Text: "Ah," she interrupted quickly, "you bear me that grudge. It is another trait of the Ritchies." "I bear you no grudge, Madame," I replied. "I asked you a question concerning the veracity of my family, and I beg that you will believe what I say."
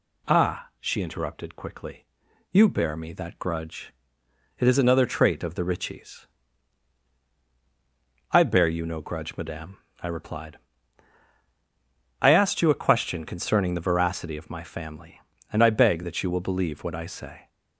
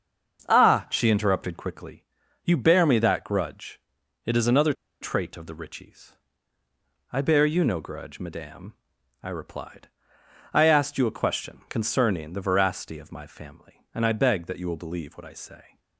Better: first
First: none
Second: starts louder than the rest; until 1.5 s; 6.5 dB // pauses between "another" and "trait"; slight; at 4.7 s; 0.28 s long

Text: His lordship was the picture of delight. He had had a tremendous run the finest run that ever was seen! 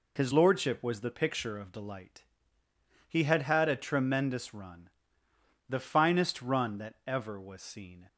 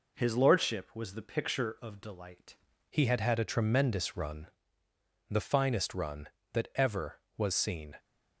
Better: first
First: pauses between "run" and "the"; noticeable; at 4.8 s; 0.80 s long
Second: changes voice at "He"; from 2.8 s on; 5.1 s long // pauses between "run" and "the"; noticeable; at 4.4 s; 0.82 s long

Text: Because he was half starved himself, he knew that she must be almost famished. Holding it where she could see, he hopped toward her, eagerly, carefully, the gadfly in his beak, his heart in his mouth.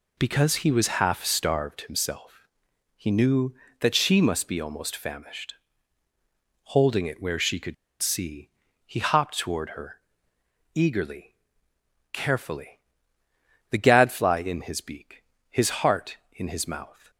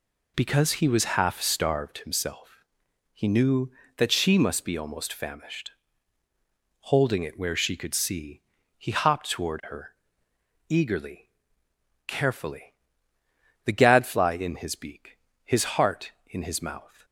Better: second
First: pauses between "could" and "see"; slight; at 7.7 s; 0.27 s long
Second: none

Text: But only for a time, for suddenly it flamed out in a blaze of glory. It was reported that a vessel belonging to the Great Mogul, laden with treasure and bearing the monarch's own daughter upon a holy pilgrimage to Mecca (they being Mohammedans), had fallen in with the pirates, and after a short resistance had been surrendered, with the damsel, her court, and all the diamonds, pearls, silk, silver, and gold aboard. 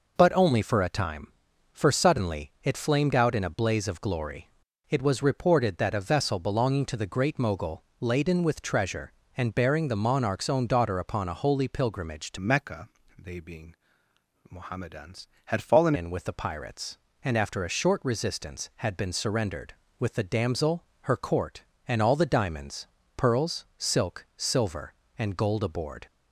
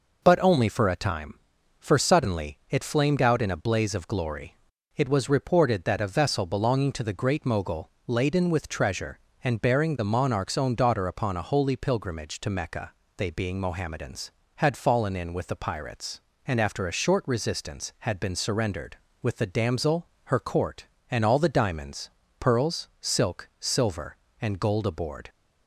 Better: second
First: changes voice from "Mecca" to "fallen"; from 12.3 to 15.9 s; 3.6 s long // pauses between "being" and "Mohammedans"; noticeable; at 13.7 s; 0.74 s long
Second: none

